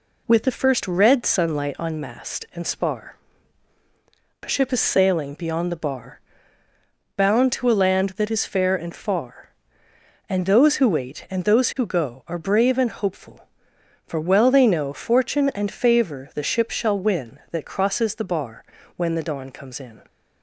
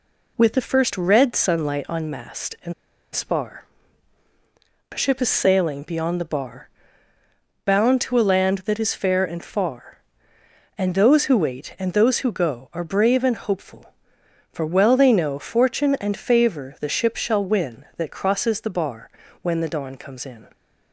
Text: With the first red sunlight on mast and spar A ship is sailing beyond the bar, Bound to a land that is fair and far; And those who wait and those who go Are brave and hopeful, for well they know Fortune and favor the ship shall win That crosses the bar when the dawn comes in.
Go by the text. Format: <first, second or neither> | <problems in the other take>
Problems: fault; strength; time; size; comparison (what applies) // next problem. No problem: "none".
first | pauses between "and" and "spar"; at 2.7 s; 0.41 s long // pauses between "spar" and "A"; strong; at 3.6 s; 1.2 s long; strong in the first // pauses between "bar" and "when"; slight; at 19.1 s; 0.32 s long; slight in the first